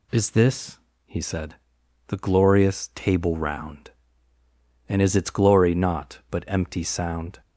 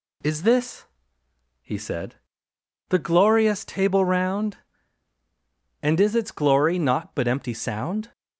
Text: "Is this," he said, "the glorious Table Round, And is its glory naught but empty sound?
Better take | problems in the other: neither | none

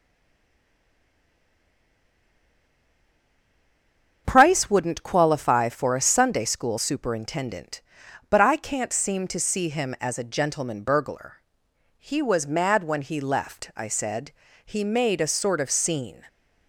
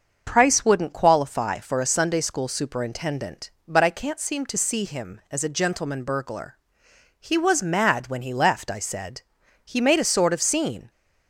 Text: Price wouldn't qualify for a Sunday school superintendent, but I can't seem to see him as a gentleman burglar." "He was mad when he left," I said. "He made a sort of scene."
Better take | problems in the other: second | stays silent before the first word; strong; until 4.2 s; 4.2 s long // starts louder than the rest; strong; until 5.2 s; 7 dB; also in the second

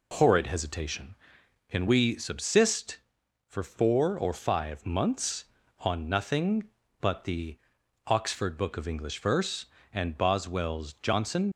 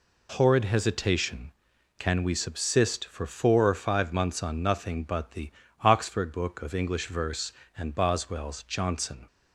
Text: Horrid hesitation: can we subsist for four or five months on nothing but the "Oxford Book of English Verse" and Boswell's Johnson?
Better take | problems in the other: second | pauses between "the" and "Oxford"; noticeable; at 7.5 s; 0.48 s long; slight in the second // leaves "Johnson" unfinished; at 11.5 s; 75 ms

